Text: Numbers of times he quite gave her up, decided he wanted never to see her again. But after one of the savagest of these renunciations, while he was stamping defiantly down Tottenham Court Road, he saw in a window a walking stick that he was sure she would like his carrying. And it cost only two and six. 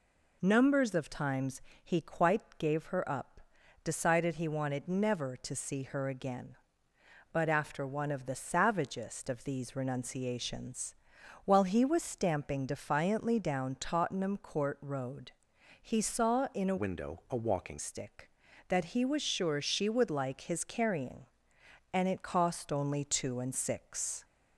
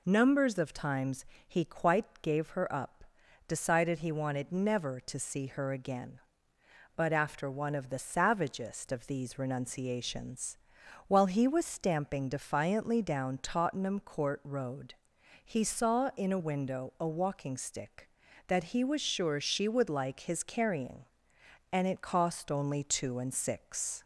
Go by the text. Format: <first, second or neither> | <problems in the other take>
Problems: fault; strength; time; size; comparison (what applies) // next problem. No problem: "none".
second | pauses between "times" and "he"; slight; at 1.5 s; 0.24 s long; slight in the second // changes voice from "window" to "walking"; from 16.7 to 17.7 s; 1.0 s long